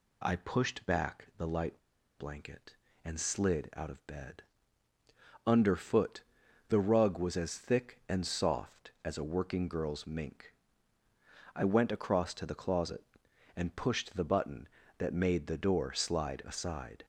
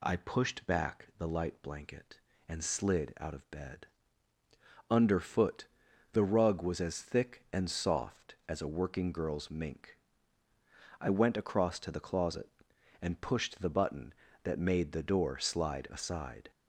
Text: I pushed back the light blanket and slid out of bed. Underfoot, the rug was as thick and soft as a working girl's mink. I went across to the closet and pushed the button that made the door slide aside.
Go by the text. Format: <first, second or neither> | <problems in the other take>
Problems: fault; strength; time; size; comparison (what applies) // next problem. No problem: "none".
second | pauses between "light" and "blanket"; at 1.8 s; 0.38 s long